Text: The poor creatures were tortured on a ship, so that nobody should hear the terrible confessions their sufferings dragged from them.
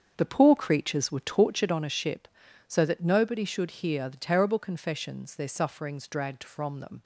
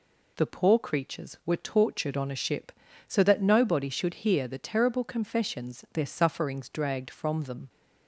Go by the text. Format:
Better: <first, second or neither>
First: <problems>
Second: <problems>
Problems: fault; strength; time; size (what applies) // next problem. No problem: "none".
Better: second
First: starts louder than the rest; strong; until 1.8 s; 7 dB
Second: none